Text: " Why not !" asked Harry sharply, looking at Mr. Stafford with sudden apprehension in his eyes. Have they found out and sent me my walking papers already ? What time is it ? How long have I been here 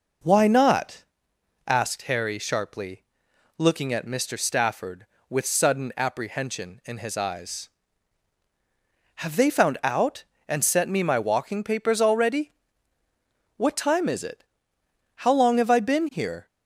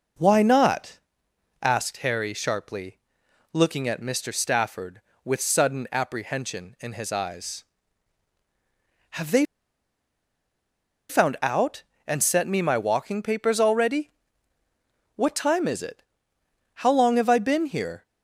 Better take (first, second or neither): first